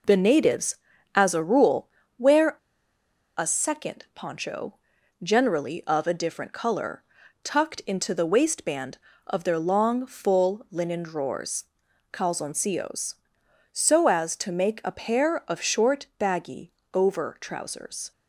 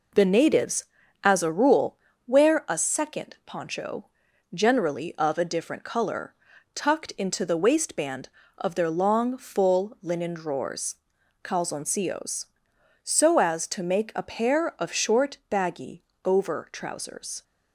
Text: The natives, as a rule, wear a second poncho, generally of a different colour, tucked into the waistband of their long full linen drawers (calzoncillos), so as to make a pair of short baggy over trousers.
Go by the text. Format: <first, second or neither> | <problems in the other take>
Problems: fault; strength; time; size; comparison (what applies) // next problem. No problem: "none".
second | pauses between "wear" and "a"; noticeable; at 2.5 s; 0.81 s long // pauses between "baggy" and "over"; slight; at 16.7 s; 0.22 s long; slight in the second